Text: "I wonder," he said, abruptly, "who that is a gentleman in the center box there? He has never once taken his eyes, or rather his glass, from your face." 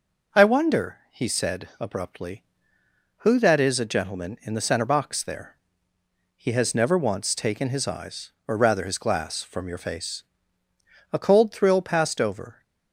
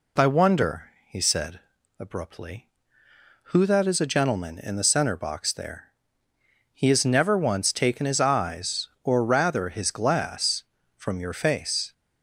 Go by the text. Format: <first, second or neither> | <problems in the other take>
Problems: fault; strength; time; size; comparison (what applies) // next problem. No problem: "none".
second | goes on to say "A cold thrill passed over"; from 11.1 s on; 1.5 s long